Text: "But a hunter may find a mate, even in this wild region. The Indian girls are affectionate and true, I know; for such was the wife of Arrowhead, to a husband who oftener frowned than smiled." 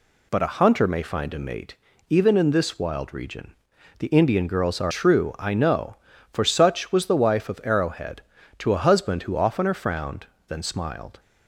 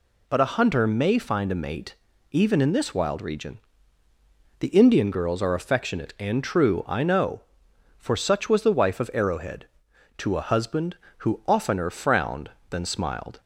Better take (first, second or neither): second